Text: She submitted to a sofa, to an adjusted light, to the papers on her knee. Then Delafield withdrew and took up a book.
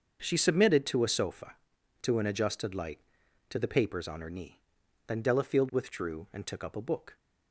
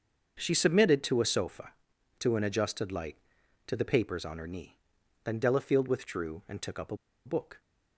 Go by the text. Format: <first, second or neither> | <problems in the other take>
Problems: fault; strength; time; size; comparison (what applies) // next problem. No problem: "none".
first | starts louder than the rest; until 1.4 s; 6.5 dB; also in the first // pauses between "a" and "book"; slight; at 6.9 s; 0.29 s long